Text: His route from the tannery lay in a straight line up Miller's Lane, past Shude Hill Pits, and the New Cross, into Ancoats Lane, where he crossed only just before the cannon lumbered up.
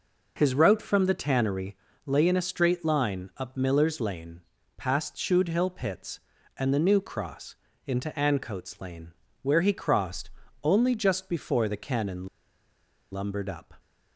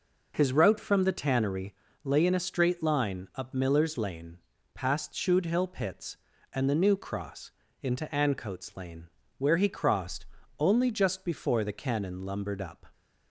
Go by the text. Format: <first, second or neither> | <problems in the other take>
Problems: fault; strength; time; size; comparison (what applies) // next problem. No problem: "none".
second | pauses between "tannery" and "lay"; slight; at 1.7 s; 0.30 s long; slight in the second // pauses between "crossed" and "only"; slight; at 10.2 s; 0.34 s long; slight in the second // pauses between "cannon" and "lumbered"; noticeable; at 12.2 s; 0.84 s long